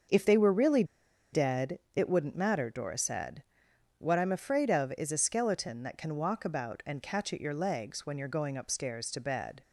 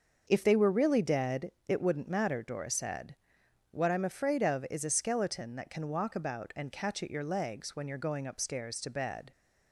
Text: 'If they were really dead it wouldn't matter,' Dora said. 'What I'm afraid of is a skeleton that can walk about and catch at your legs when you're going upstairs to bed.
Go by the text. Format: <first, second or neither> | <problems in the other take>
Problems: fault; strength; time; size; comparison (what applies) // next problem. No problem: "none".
second | starts louder than the rest; until 1.5 s; 6.5 dB; also in the second // pauses between "really" and "dead"; noticeable; at 0.8 s; 0.49 s long // pauses between "dead" and "it"; slight; at 1.7 s; 0.16 s long; slight in the second